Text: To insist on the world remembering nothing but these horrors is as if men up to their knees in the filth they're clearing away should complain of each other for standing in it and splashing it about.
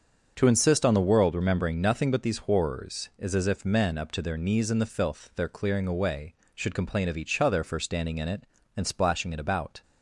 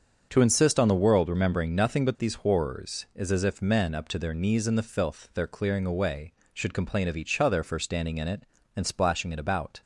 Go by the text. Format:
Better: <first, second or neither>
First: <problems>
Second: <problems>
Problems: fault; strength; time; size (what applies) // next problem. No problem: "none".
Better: neither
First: starts louder than the rest; until 1.3 s; 6.5 dB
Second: starts louder than the rest; until 1.3 s; 6.5 dB